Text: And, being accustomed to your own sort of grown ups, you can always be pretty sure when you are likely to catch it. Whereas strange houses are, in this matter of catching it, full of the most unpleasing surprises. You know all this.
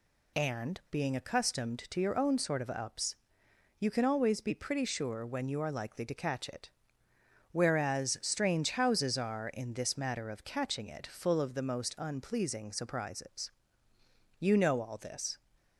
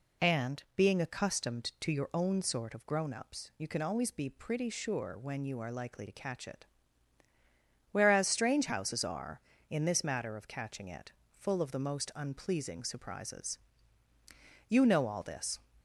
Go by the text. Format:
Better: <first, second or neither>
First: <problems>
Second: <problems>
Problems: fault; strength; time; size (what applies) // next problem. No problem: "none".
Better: second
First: skips "grown"; at 2.6 s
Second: none